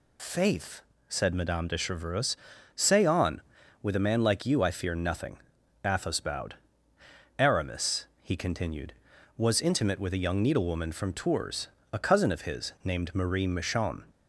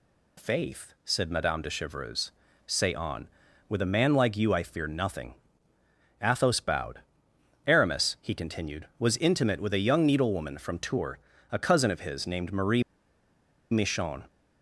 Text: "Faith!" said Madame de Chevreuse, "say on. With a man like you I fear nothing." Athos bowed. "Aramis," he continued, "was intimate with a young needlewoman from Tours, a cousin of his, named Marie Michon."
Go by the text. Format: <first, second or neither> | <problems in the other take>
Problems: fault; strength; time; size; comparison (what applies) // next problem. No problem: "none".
first | pauses between "Marie" and "Michon"; noticeable; at 12.8 s; 0.90 s long